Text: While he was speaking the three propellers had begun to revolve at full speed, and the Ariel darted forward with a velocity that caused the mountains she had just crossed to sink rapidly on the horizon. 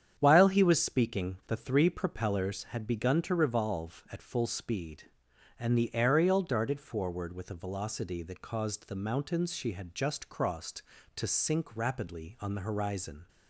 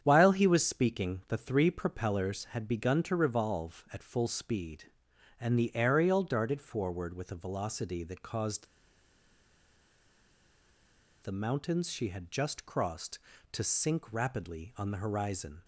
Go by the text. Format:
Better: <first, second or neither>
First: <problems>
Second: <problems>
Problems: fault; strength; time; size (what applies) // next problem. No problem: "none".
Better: first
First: starts louder than the rest; strong; until 1.1 s; 8.5 dB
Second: starts louder than the rest; strong; until 1.0 s; 8.5 dB // pauses between "caused" and "the"; strong; at 8.6 s; 2.5 s long